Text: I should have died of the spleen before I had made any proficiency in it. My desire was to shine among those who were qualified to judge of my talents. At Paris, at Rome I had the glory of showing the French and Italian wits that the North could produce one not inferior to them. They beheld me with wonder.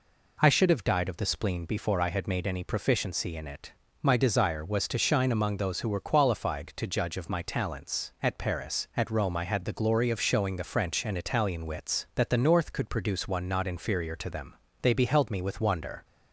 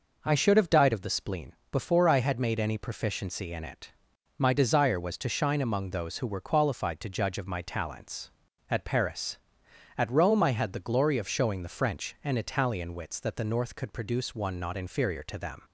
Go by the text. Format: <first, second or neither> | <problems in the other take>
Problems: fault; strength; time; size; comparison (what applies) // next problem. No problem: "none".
first | pauses between "spleen" and "before"; slight; at 1.5 s; 0.16 s long // stops before "They beheld me with wonder"; at 15.6 s